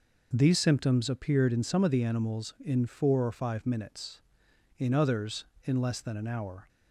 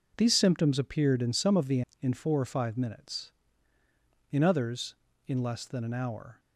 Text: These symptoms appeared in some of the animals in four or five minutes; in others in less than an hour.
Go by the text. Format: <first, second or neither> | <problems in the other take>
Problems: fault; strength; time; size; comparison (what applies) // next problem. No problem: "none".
first | skips "animals"; at 1.9 s